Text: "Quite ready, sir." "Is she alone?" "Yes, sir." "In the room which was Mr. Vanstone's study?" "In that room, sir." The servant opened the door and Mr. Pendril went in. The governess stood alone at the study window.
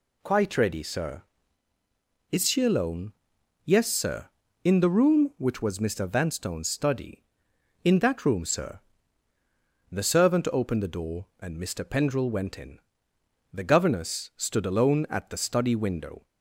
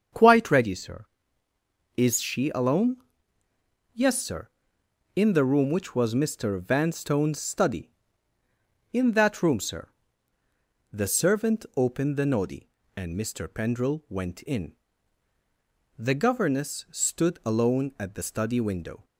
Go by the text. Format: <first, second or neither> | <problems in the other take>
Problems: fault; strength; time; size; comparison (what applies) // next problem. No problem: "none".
first | starts louder than the rest; strong; until 2.0 s; 7 dB // says "noddy" for "door"; at 12.2 s